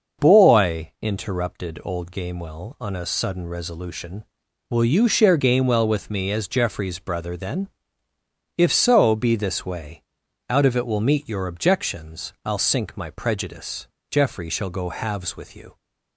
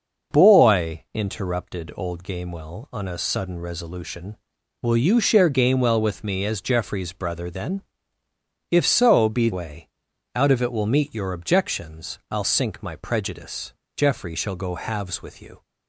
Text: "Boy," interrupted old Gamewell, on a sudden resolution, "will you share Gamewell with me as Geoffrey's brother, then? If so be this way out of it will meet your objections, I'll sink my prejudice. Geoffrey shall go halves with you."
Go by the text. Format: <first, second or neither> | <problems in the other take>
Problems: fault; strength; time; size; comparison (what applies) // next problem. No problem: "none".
first | starts louder than the rest; until 1.4 s; 6 dB; noticeable in the first // skips "this"; at 9.5 s // pauses between "way" and "out"; noticeable; at 9.8 s; 0.48 s long; noticeable in the first